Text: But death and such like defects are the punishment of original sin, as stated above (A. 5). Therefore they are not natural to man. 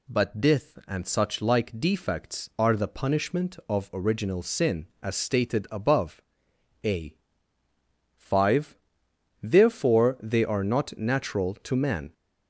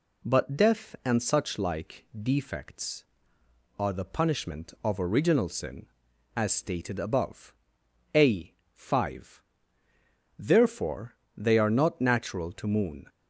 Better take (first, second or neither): first